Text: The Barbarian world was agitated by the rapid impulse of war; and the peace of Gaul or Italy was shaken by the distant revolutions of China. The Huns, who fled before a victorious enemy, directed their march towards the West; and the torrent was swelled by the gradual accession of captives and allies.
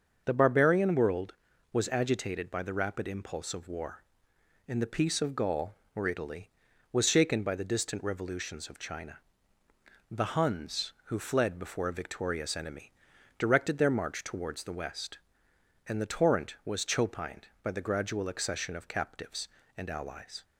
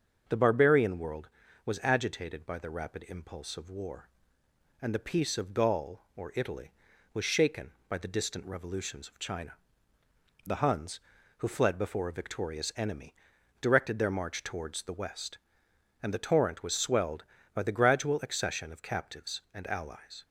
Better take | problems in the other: second | starts louder than the rest; until 1.2 s; 6.5 dB; also in the second // says "chopined" for "swelled"; at 16.8 s

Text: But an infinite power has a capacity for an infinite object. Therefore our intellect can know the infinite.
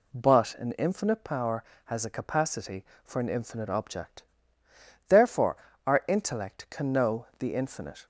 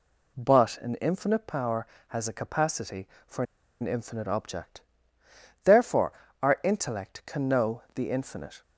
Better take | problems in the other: first | pauses between "for" and "an"; at 3.4 s; 0.36 s long // pauses between "Therefore" and "our"; slight; at 6.1 s; 0.32 s long; slight in the first

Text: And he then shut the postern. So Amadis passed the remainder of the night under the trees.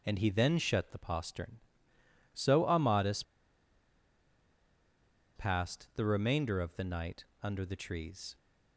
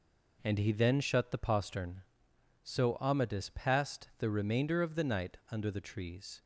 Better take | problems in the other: second | pauses between "Amadis" and "passed"; strong; at 3.2 s; 2.1 s long // pauses between "night" and "under"; slight; at 7.2 s; 0.18 s long

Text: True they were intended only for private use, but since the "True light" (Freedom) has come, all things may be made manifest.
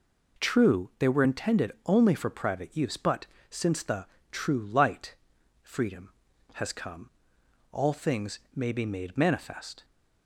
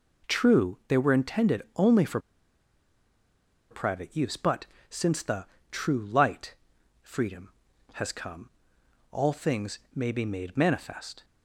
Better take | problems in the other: first | pauses between "for" and "private"; strong; at 2.1 s; 1.5 s long // pauses between "but" and "since"; slight; at 4.6 s; 0.24 s long; slight in the first // pauses between "the" and "True"; slight; at 5.4 s; 0.26 s long; slight in the first

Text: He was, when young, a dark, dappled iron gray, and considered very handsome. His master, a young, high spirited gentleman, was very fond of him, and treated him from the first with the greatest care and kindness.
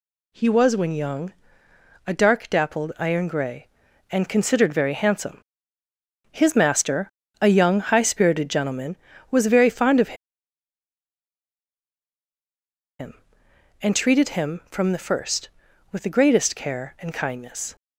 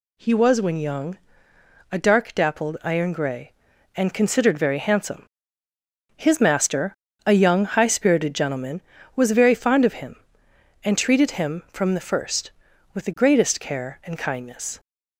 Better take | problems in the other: second | pauses between "of" and "him"; strong; at 10.1 s; 2.8 s long

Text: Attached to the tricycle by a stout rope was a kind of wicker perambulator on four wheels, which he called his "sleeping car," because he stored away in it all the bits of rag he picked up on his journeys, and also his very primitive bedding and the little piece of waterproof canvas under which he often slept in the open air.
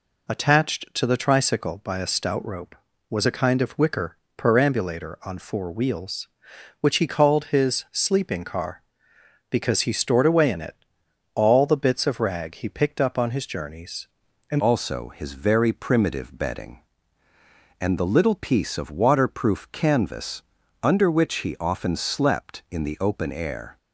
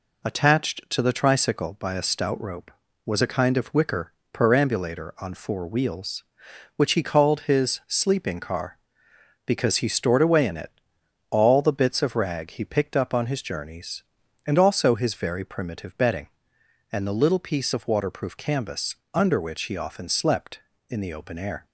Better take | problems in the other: second | pauses between "wicker" and "perambulator"; slight; at 4.1 s; 0.18 s long; slight in the second // pauses between "it" and "all"; noticeable; at 10.7 s; 0.58 s long; noticeable in the second // changes voice at "also"; from 14.5 s on; 9.2 s long // pauses between "canvas" and "under"; at 20.4 s; 0.38 s long; slight in the second

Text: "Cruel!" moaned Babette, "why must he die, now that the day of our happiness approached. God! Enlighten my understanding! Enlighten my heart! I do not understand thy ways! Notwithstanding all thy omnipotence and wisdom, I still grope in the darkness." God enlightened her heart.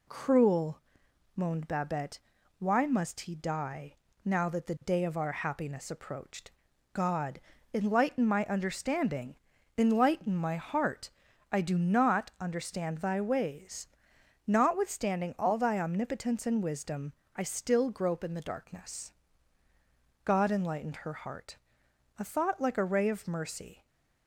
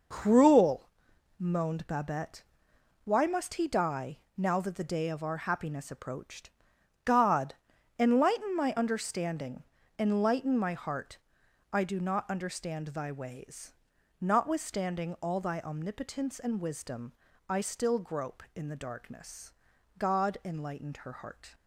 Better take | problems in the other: second | goes on to say "A thought like a ray of mercy"; strong; from 22.1 s on; 1.6 s long

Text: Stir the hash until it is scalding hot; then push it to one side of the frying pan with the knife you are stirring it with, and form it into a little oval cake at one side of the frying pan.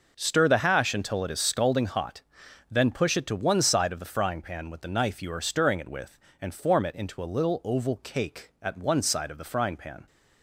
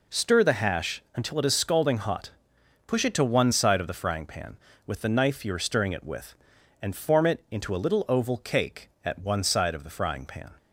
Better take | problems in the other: first | skips "then"; at 2.5 s

